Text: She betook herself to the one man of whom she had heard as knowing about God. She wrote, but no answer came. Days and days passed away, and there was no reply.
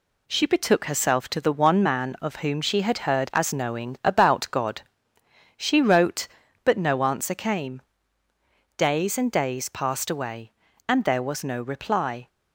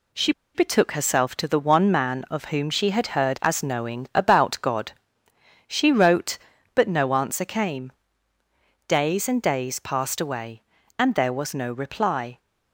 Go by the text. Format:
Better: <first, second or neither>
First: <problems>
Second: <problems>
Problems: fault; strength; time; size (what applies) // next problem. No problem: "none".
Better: first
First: none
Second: pauses between "She" and "betook"; slight; at 0.3 s; 0.23 s long